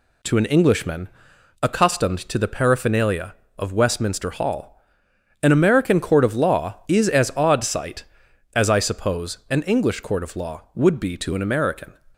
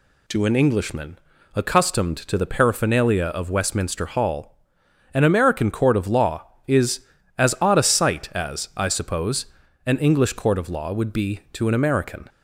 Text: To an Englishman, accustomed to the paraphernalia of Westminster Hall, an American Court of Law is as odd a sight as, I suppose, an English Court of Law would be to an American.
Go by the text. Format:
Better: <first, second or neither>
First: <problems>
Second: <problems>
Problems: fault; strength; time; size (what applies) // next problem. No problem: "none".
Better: second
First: skips "a"; at 7.6 s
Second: none